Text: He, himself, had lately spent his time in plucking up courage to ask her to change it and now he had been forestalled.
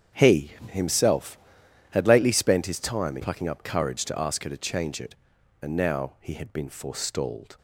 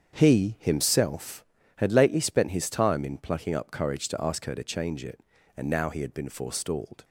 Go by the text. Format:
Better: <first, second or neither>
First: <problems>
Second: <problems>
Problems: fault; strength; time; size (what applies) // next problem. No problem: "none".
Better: second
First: starts louder than the rest; strong; until 1.3 s; 8.5 dB // skips "in"; at 3.1 s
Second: starts louder than the rest; strong; until 1.2 s; 7.5 dB